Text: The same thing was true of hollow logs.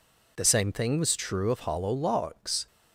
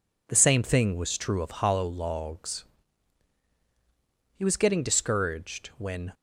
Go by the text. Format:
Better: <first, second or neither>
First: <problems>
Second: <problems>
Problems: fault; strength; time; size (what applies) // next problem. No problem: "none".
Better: first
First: none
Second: goes on to say "He was getting discouraged when"; strong; from 4.3 s on; 1.7 s long